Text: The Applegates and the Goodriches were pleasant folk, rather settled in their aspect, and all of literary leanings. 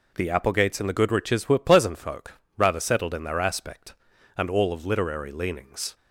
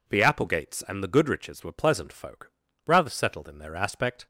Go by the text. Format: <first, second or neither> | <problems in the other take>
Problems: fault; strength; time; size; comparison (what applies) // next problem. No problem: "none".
first | stops before "and all of literary leanings"; at 4.2 s